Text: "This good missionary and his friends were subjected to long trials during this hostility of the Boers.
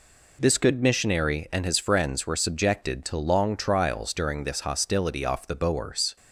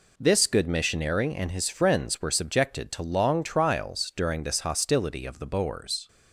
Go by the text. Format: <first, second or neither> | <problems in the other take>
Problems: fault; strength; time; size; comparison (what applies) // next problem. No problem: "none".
second | says "off" for "of"; at 5.2 s